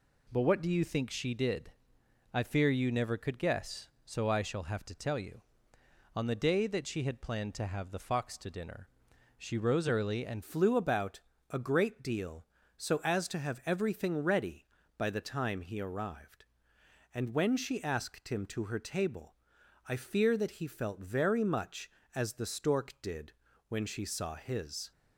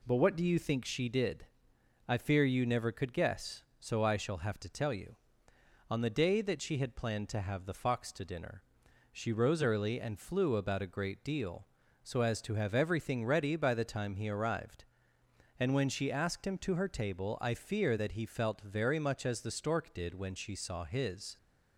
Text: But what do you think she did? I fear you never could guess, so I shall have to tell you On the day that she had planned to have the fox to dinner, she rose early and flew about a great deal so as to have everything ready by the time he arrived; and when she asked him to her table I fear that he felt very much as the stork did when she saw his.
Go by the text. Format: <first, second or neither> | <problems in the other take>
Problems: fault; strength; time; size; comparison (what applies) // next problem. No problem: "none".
second | changes voice at "flew"; from 10.4 s on; 14.5 s long // pauses between "about" and "a"; slight; at 11.2 s; 0.28 s long // pauses between "table" and "I"; noticeable; at 19.3 s; 0.52 s long // pauses between "did" and "when"; at 23.3 s; 0.38 s long